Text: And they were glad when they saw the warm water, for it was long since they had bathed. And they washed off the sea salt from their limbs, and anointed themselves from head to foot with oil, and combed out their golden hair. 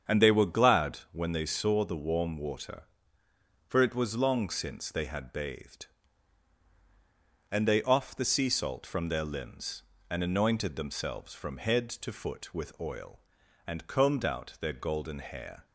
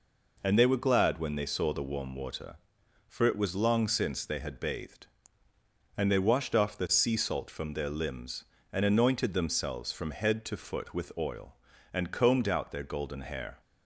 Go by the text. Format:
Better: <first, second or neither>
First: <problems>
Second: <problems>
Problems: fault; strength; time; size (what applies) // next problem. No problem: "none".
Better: second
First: starts louder than the rest; strong; until 1.2 s; 7.5 dB // skips "washed"; at 7.8 s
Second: none